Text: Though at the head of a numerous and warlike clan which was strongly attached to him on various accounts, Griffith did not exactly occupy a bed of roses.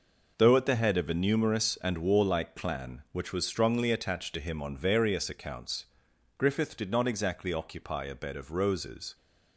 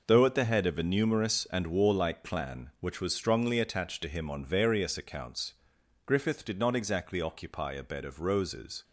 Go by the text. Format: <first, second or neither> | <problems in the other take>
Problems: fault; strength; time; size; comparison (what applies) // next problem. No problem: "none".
neither | none